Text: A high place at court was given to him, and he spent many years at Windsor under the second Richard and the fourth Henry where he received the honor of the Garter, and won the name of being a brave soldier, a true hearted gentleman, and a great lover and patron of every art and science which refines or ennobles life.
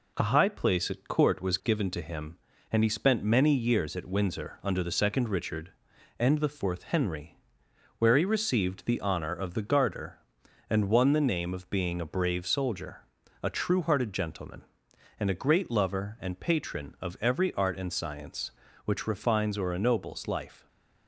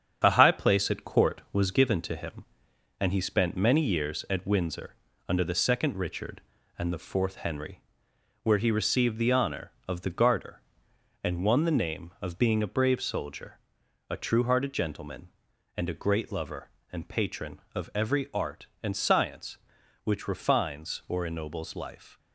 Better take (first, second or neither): first